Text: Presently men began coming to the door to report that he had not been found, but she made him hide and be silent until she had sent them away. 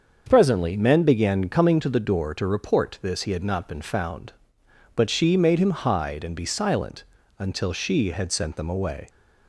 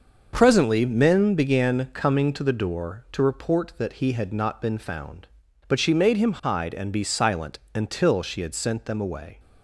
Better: second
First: starts louder than the rest; until 1.2 s; 6.5 dB // says "this" for "that"; at 3.0 s // pauses between "silent" and "until"; slight; at 7.0 s; 0.34 s long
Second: starts louder than the rest; until 1.3 s; 6 dB // pauses between "silent" and "until"; slight; at 7.5 s; 0.16 s long

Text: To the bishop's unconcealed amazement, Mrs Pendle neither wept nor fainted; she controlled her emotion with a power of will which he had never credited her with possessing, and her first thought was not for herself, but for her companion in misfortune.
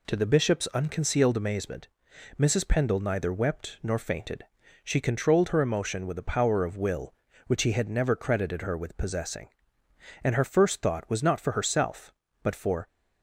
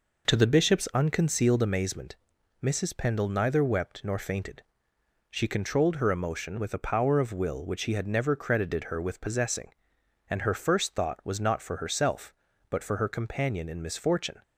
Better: second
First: stops before "her companion in misfortune"; at 12.8 s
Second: none

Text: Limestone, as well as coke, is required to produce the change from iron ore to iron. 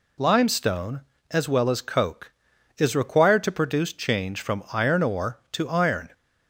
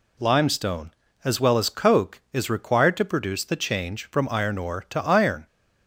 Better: second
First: skips "the"; at 3.9 s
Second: none

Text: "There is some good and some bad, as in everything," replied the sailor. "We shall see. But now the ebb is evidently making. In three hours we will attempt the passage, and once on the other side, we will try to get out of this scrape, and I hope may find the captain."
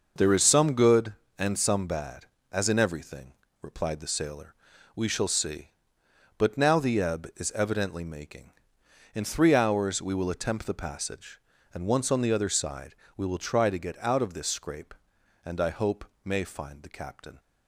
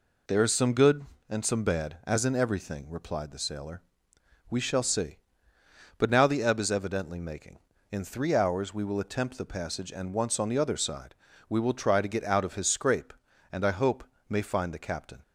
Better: first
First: pauses between "hope" and "may"; slight; at 16.0 s; 0.22 s long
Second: says "his" for "this"; at 12.5 s // pauses between "hope" and "may"; slight; at 14.0 s; 0.26 s long

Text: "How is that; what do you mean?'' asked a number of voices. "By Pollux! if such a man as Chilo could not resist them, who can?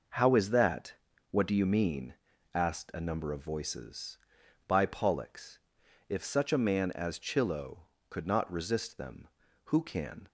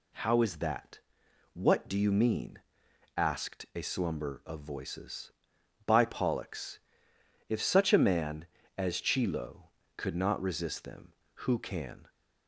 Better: first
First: none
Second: says "slumber" for "number"; at 3.8 s

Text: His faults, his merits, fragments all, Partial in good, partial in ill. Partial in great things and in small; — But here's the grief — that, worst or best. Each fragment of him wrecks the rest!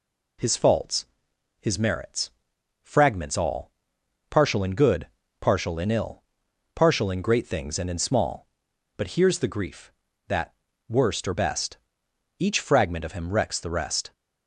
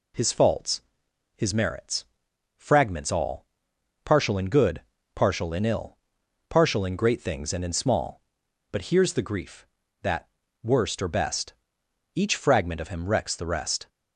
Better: neither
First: none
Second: none

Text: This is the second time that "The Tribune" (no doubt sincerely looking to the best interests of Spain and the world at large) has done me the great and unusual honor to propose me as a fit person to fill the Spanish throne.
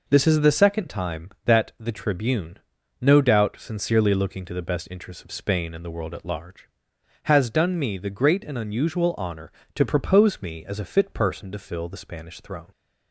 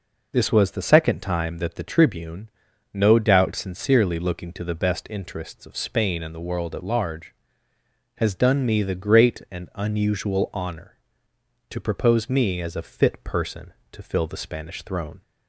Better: first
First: none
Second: says "was" for "is"; at 0.5 s

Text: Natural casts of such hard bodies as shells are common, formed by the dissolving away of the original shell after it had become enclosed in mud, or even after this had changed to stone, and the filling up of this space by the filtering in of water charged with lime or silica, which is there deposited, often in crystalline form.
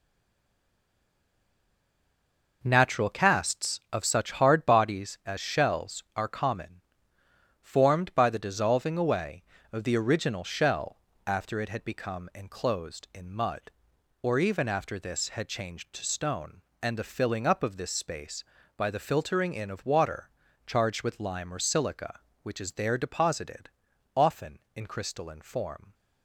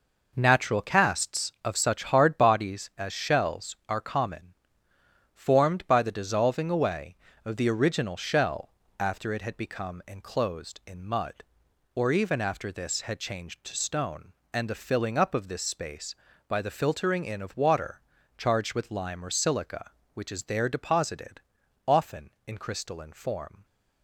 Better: second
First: stays silent before the first word; strong; until 2.6 s; 2.6 s long // pauses between "shell" and "after"; slight; at 10.9 s; 0.26 s long // pauses between "water" and "charged"; at 20.2 s; 0.38 s long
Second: pauses between "shell" and "after"; slight; at 8.7 s; 0.26 s long // pauses between "water" and "charged"; at 18.0 s; 0.38 s long

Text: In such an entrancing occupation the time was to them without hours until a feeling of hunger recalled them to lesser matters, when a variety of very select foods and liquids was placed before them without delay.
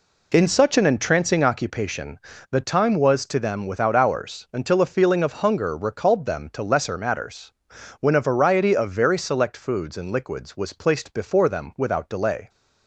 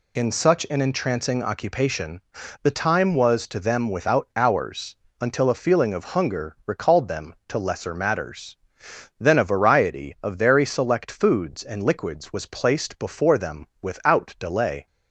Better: first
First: pauses between "occupation" and "the"; slight; at 2.1 s; 0.30 s long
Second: pauses between "occupation" and "the"; at 2.2 s; 0.40 s long // pauses between "hours" and "until"; slight; at 4.9 s; 0.24 s long // says "then" for "when"; at 9.2 s // pauses between "them" and "without"; slight; at 13.6 s; 0.16 s long

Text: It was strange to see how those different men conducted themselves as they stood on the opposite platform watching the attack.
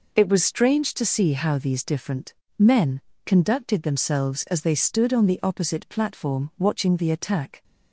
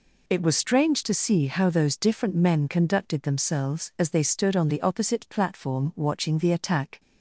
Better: second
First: says "these" for "those"; at 1.5 s // pauses between "different" and "men"; slight; at 2.3 s; 0.26 s long // pauses between "men" and "conducted"; slight; at 2.9 s; 0.26 s long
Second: none

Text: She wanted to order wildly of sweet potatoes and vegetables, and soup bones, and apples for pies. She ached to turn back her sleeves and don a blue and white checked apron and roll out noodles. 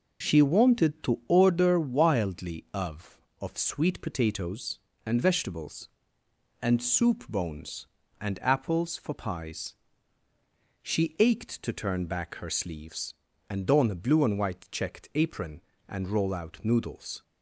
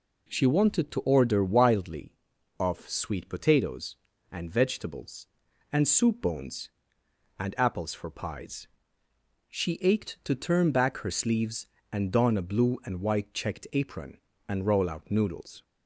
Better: second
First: says "of" twice; at 3.4 s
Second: none

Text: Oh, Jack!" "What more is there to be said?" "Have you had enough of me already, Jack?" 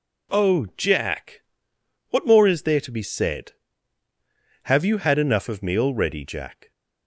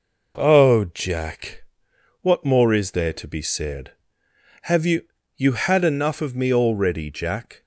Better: first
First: none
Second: says "you" twice; at 5.3 s

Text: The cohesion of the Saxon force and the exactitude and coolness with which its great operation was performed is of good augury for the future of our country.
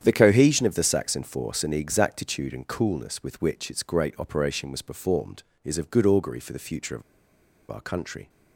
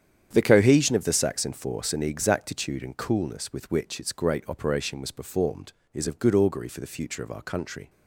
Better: second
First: starts louder than the rest; strong; until 1.0 s; 9 dB // pauses between "of" and "our"; noticeable; at 7.0 s; 0.68 s long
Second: starts louder than the rest; strong; until 1.3 s; 9 dB

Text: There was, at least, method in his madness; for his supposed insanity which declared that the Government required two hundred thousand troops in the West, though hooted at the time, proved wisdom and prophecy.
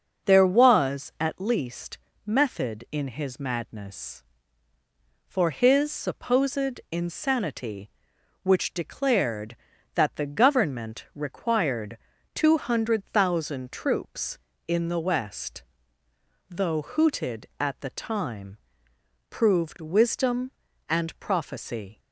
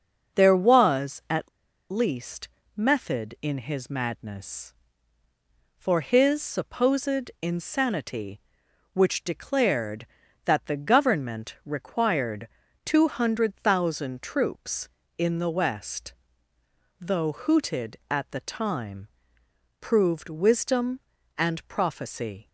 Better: first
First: starts louder than the rest; noticeable; until 1.3 s; 6 dB // pauses between "required" and "two"; at 11.9 s; 0.38 s long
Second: starts louder than the rest; noticeable; until 1.4 s; 6 dB // pauses between "at" and "least"; at 1.4 s; 0.42 s long // pauses between "required" and "two"; at 12.4 s; 0.38 s long

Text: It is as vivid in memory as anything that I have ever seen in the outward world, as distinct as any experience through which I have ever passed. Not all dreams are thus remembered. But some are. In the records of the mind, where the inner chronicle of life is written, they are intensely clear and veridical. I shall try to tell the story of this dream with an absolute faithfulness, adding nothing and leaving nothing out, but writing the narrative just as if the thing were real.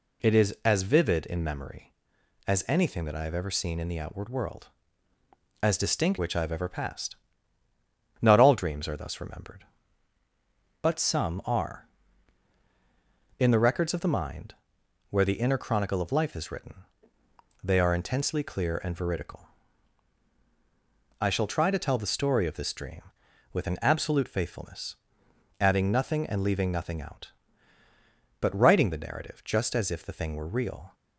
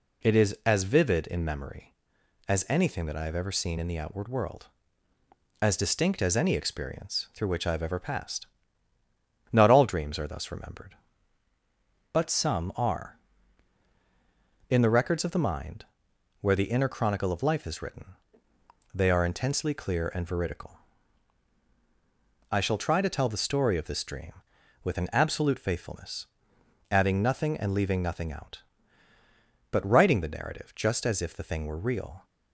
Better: second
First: skips "as any experience through"; at 6.1 s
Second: none

